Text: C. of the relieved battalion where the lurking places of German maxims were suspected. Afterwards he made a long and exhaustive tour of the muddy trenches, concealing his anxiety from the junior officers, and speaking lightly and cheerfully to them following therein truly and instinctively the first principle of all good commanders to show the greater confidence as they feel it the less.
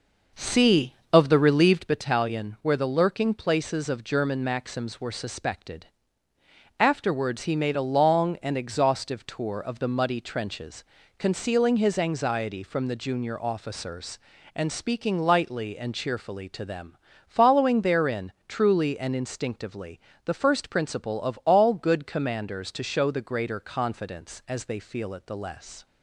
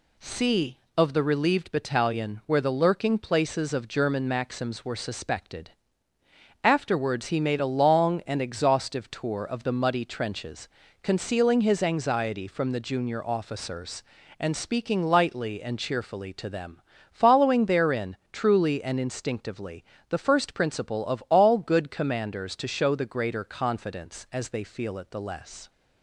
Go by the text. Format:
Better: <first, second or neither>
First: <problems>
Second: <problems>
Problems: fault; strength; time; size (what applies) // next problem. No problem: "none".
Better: second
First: starts louder than the rest; noticeable; until 2.1 s; 5.5 dB // pauses between "them" and "following"; slight; at 16.9 s; 0.30 s long // pauses between "therein" and "truly"; slight; at 18.3 s; 0.16 s long // pauses between "instinctively" and "the"; slight; at 19.9 s; 0.26 s long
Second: pauses between "them" and "following"; slight; at 16.8 s; 0.30 s long // pauses between "therein" and "truly"; slight; at 18.1 s; 0.16 s long // pauses between "instinctively" and "the"; slight; at 19.8 s; 0.26 s long